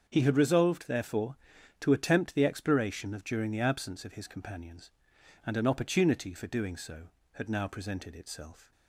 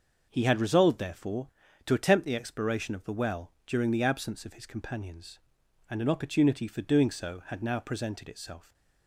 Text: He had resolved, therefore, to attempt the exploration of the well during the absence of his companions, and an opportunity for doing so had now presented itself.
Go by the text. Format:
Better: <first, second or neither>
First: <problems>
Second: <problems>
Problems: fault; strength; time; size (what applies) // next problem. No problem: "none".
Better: second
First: starts louder than the rest; until 1.0 s; 7 dB // skips "the well"; at 3.2 s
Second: starts louder than the rest; until 1.3 s; 6.5 dB